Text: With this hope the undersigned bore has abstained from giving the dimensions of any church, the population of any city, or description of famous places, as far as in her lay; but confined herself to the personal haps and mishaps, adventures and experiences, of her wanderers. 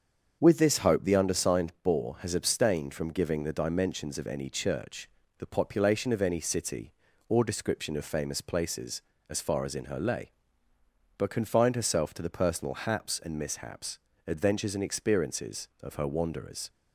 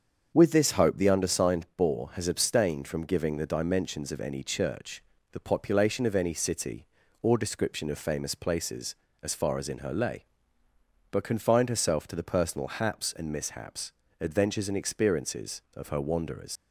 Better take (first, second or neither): first